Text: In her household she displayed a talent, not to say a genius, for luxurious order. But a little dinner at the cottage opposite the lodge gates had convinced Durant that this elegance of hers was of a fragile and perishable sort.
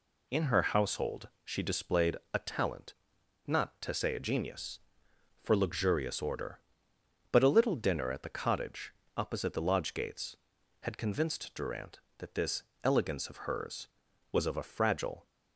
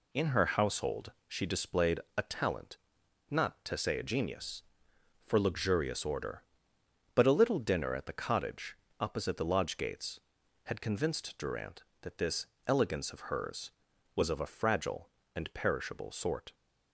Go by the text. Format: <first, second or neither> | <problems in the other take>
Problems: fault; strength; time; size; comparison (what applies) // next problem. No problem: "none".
second | pauses between "household" and "she"; slight; at 1.2 s; 0.16 s long; slight in the second // pauses between "displayed" and "a"; slight; at 2.1 s; 0.18 s long; slight in the second // pauses between "cottage" and "opposite"; slight; at 8.9 s; 0.24 s long; slight in the second // pauses between "this" and "elegance"; slight; at 12.6 s; 0.20 s long; slight in the second // stops before "and perishable sort"; at 15.2 s